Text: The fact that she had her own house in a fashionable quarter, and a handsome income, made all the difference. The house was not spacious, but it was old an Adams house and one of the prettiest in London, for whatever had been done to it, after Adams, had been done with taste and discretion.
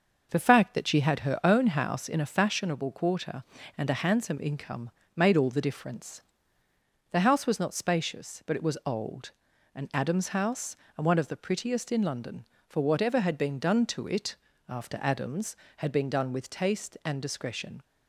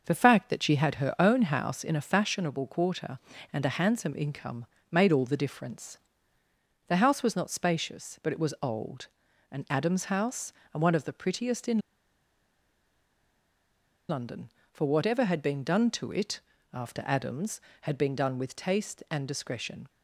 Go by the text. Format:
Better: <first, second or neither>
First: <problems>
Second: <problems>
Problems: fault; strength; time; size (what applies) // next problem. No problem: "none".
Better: first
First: pauses between "old" and "an"; at 9.3 s; 0.42 s long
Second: pauses between "old" and "an"; at 9.0 s; 0.42 s long // pauses between "in" and "London"; strong; at 11.7 s; 2.3 s long